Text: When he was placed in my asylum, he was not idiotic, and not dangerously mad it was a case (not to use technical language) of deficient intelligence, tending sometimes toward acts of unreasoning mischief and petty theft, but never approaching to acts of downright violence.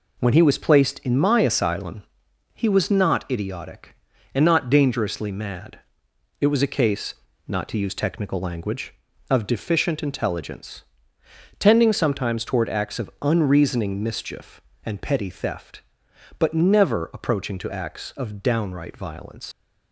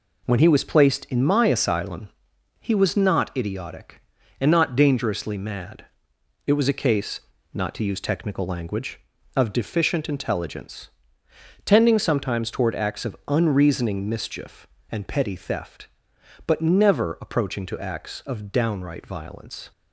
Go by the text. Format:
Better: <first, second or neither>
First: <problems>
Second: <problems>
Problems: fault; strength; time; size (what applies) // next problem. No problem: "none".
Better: second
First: pauses between "mad" and "it"; noticeable; at 5.7 s; 0.62 s long // leaves "violence" unfinished; at 19.5 s; 100 ms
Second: pauses between "mad" and "it"; noticeable; at 5.8 s; 0.62 s long